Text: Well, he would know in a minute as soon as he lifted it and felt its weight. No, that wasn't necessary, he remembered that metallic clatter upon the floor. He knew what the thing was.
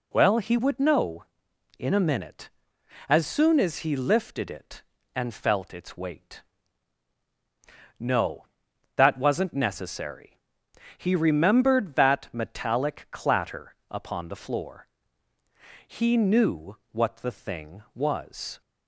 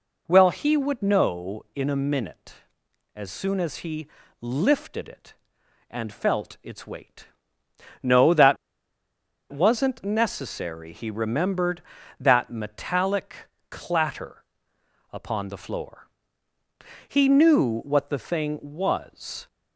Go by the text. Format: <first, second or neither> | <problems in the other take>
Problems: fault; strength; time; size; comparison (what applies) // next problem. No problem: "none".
first | pauses between "he" and "lifted"; slight; at 4.0 s; 0.34 s long // pauses between "that" and "wasn't"; noticeable; at 8.5 s; 0.96 s long // pauses between "metallic" and "clatter"; at 13.3 s; 0.38 s long // pauses between "clatter" and "upon"; noticeable; at 14.4 s; 0.68 s long